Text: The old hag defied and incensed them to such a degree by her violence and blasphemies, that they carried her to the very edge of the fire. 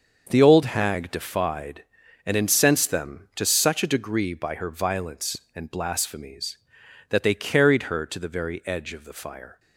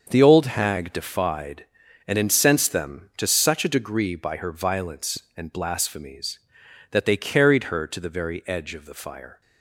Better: neither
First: starts louder than the rest; until 1.3 s; 6.5 dB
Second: starts louder than the rest; until 1.1 s; 6.5 dB

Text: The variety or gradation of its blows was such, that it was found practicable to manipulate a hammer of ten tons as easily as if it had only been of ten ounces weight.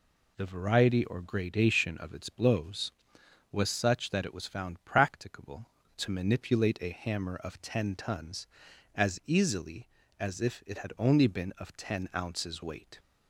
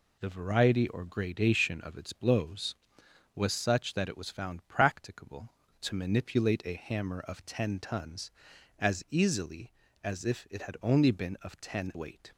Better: first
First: none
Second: skips "ounces"; at 11.9 s

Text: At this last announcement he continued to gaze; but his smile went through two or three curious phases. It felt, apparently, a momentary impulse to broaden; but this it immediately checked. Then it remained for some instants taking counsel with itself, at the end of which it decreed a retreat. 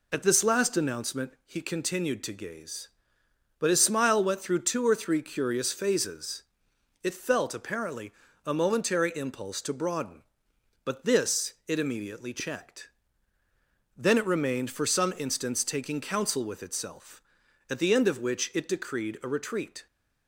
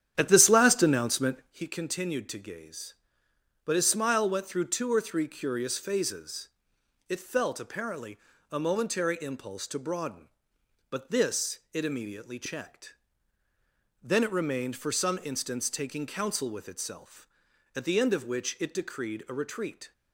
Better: first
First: none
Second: starts louder than the rest; strong; until 1.6 s; 10 dB

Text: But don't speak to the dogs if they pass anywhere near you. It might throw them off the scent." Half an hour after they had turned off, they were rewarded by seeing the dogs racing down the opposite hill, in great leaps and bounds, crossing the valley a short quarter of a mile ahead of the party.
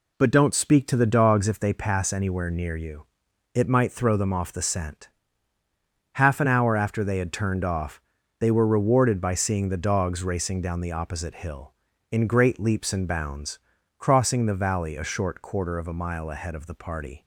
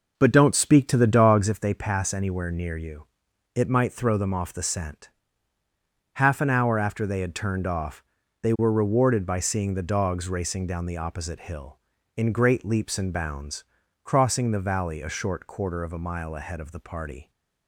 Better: first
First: none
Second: starts louder than the rest; noticeable; until 1.6 s; 5.5 dB

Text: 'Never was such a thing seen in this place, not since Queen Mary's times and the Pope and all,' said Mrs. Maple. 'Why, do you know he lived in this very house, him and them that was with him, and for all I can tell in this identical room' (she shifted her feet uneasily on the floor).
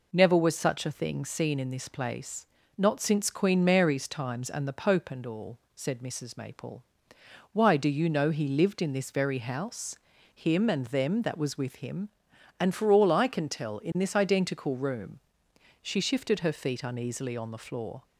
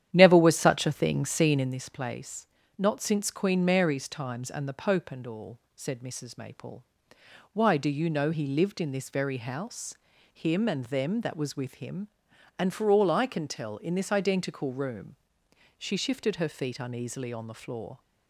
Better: first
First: none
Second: starts louder than the rest; strong; until 1.8 s; 10.5 dB

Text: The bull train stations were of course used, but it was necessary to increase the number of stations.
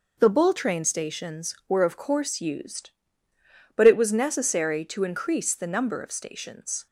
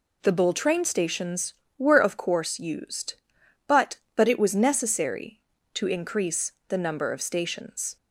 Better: first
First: none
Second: says "but" twice; at 4.1 s // pauses between "increase" and "the"; slight; at 6.5 s; 0.16 s long

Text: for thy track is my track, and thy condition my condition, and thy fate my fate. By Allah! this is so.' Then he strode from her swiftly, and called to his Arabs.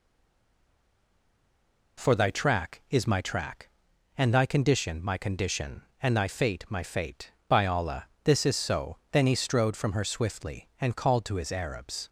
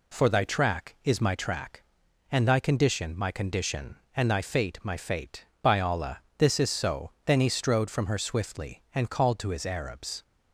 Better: second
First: stays silent before the first word; noticeable; until 1.9 s; 1.9 s long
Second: none

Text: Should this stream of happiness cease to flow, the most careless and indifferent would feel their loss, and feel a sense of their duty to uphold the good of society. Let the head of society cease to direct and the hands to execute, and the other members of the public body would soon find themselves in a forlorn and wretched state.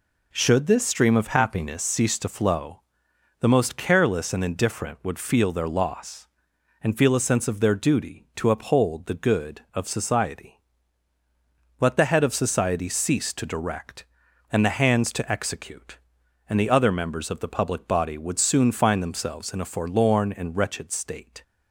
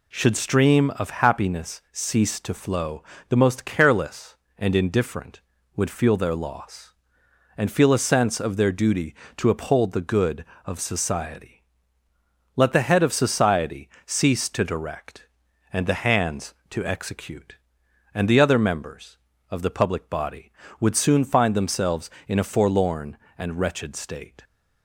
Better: first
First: none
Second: skips "this"; at 0.3 s // pauses between "society" and "cease"; slight; at 13.8 s; 0.18 s long

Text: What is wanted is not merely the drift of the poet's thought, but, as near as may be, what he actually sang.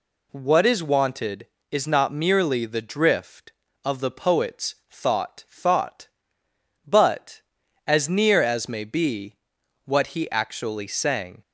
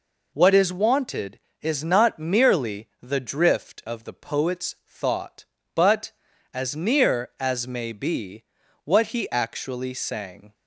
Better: second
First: pauses between "poet's" and "thought"; slight; at 4.7 s; 0.16 s long // says "thought" twice; at 5.4 s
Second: none

